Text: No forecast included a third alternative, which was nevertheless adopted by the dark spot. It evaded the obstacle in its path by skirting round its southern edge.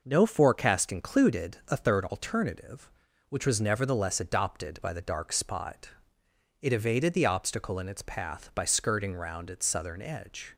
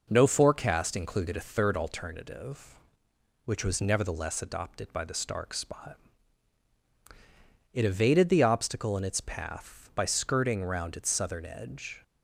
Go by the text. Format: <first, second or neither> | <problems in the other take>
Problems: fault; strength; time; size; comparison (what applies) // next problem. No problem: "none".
first | says "stark" for "dark"; at 5.1 s